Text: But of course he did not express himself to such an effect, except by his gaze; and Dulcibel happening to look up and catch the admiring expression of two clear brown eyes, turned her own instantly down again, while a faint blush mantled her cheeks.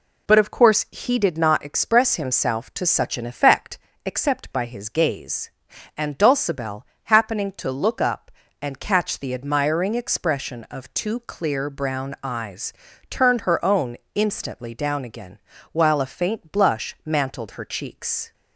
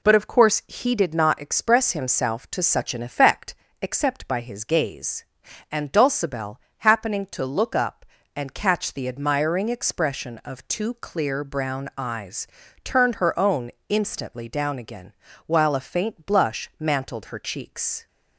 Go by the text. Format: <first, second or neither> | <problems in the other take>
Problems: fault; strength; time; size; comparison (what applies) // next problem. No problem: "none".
neither | pauses between "Dulcibel" and "happening"; slight; the same in both // pauses between "own" and "instantly"; slight; the same in both